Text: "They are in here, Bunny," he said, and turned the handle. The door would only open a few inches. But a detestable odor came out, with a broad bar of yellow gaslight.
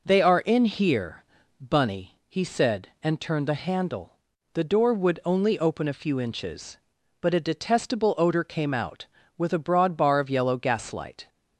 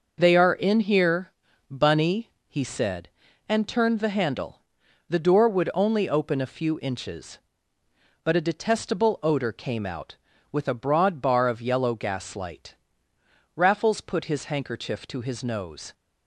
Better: first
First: none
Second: goes on to say "Raffles put his handkerchief to his nose"; strong; from 13.5 s on; 2.3 s long

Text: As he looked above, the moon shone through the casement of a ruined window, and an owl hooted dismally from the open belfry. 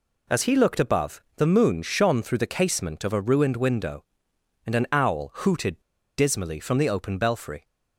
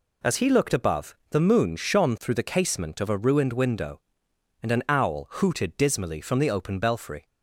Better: second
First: pauses between "hooted" and "dismally"; at 5.7 s; 0.38 s long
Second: none

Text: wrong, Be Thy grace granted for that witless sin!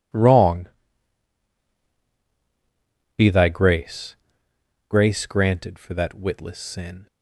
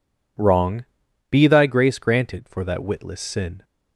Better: second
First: says "grace" twice; at 4.8 s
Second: none

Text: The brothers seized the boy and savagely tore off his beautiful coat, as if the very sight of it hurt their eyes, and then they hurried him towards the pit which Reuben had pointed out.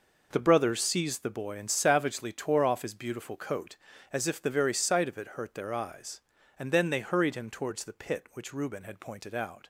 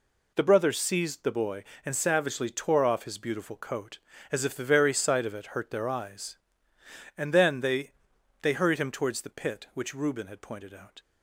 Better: first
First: none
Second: says "they" twice; at 8.4 s

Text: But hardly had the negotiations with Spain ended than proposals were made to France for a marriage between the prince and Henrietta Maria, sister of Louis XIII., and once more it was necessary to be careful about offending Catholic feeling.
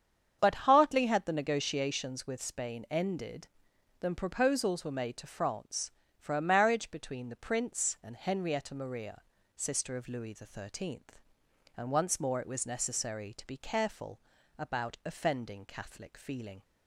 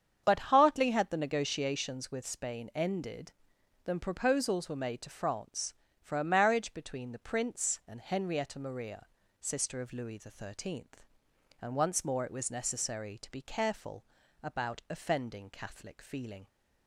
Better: neither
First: starts louder than the rest; strong; until 1.4 s; 8 dB // pauses between "careful" and "about"; at 14.2 s; 0.38 s long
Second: starts louder than the rest; strong; until 1.2 s; 8 dB // pauses between "careful" and "about"; at 14.0 s; 0.38 s long

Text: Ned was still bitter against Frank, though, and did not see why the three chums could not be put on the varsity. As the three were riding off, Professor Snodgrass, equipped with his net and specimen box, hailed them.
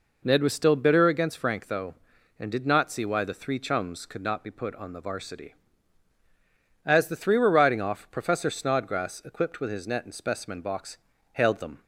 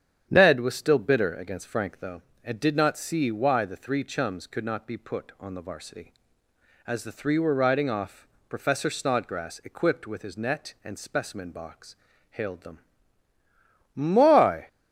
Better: first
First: none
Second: starts louder than the rest; strong; until 1.3 s; 9 dB // goes on to say "My"; noticeable; from 13.9 s on; 0.74 s long

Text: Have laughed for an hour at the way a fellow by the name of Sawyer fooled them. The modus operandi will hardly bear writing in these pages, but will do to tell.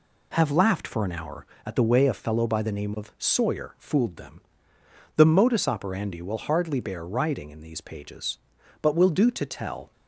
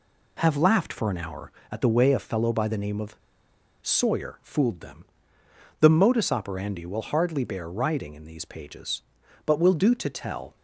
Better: first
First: none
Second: pauses between "of" and "Sawyer"; noticeable; at 3.1 s; 0.67 s long

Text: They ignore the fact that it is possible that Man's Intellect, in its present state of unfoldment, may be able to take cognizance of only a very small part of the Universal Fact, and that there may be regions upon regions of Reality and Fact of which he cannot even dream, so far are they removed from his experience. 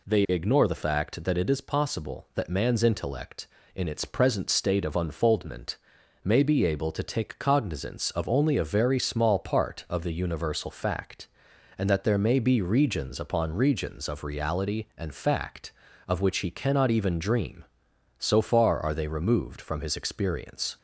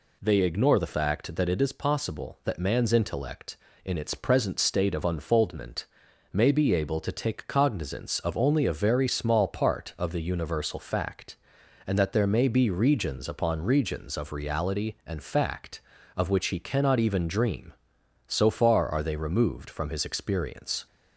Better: neither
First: none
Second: none

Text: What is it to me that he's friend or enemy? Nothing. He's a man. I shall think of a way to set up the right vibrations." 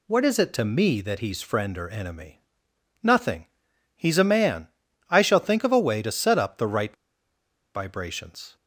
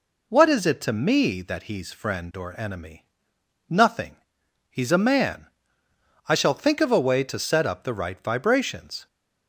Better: second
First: pauses between "right" and "vibrations"; noticeable; at 6.9 s; 0.80 s long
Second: none

